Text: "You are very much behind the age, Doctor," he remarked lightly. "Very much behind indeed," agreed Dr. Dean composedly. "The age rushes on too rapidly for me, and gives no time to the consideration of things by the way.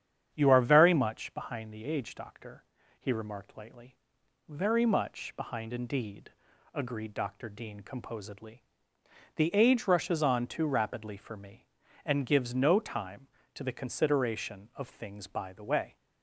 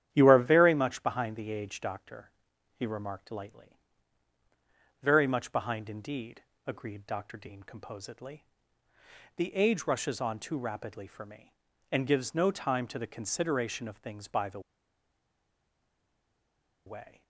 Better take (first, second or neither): first